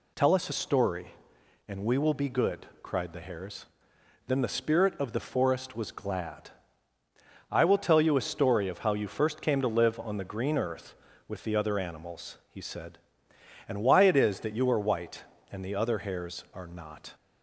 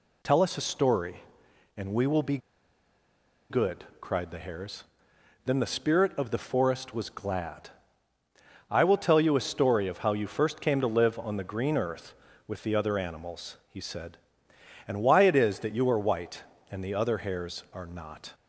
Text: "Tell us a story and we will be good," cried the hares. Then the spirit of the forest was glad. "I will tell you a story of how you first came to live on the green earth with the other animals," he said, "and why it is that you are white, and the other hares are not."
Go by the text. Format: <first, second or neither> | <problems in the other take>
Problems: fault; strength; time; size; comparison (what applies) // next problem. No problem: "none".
first | pauses between "be" and "good"; at 2.3 s; 1.1 s long